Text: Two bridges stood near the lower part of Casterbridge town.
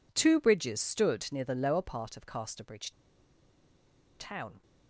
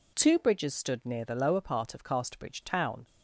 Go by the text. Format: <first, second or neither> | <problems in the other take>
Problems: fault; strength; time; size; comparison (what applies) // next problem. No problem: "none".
second | pauses between "Casterbridge" and "town"; strong; at 2.8 s; 1.2 s long